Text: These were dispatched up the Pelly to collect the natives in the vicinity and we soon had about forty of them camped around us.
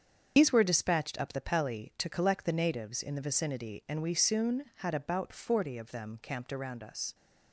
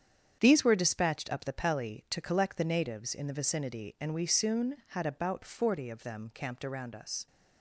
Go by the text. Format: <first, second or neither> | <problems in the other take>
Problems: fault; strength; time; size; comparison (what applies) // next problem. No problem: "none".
second | loses the start of "These"; at 0.3 s; 75 ms // starts louder than the rest; strong; until 1.3 s; 7 dB; strong in the second